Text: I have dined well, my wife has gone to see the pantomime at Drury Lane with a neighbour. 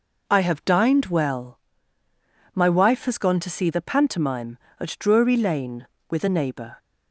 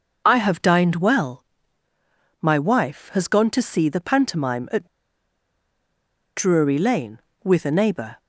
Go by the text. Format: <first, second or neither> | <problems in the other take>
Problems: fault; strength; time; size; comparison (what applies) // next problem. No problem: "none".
first | pauses between "at" and "Drury"; strong; at 4.8 s; 1.5 s long